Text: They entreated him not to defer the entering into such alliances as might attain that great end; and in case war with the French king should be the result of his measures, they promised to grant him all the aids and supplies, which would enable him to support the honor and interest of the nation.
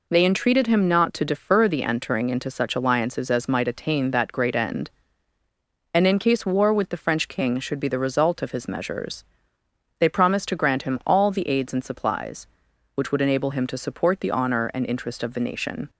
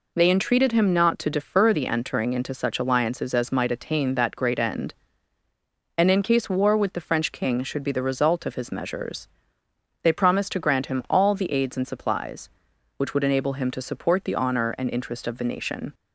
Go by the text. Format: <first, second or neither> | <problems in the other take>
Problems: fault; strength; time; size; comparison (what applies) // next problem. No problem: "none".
neither | none